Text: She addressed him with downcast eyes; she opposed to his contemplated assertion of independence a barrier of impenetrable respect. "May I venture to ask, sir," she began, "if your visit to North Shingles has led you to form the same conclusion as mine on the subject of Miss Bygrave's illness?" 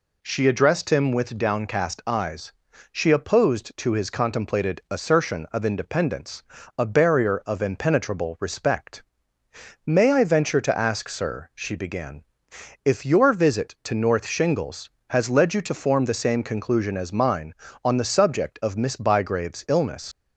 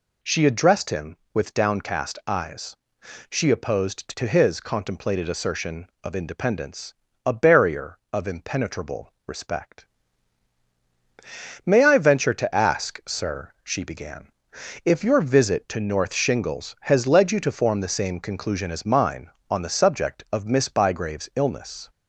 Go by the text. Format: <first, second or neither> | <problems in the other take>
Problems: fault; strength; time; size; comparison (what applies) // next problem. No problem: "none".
second | pauses between "independence" and "a"; slight; at 6.4 s; 0.34 s long; slight in the second // leaves "illness" unfinished; at 20.1 s; 70 ms